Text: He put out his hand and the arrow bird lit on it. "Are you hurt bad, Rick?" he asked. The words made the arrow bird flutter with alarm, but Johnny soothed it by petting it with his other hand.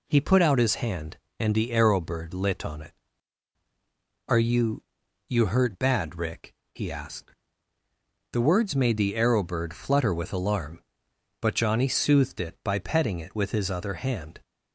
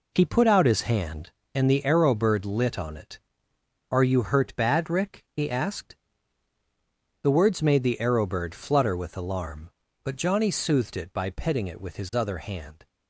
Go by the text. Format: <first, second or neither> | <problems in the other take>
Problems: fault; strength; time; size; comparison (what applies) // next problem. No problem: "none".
second | says "you" twice; at 5.2 s